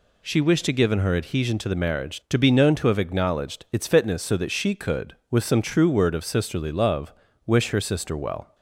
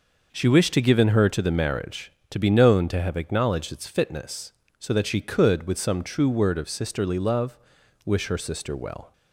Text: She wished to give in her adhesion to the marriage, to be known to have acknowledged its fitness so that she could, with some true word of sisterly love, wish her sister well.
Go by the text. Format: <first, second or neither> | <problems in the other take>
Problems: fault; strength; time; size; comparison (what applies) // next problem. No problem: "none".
first | skips "adhesion"; at 1.2 s